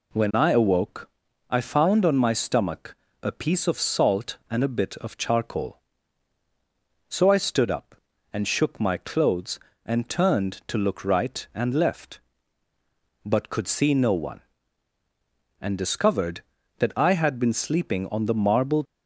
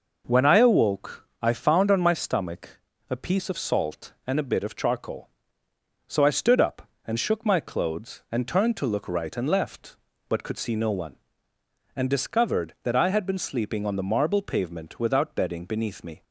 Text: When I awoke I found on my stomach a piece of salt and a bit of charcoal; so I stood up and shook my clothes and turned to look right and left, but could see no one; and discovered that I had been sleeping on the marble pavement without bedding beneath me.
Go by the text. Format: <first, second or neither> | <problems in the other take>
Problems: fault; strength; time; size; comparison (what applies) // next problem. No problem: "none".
second | pauses between "awoke" and "I"; at 1.1 s; 0.40 s long // pauses between "stomach" and "a"; slight; at 2.9 s; 0.26 s long; slight in the second // stops before "pavement without bedding beneath me"; at 18.8 s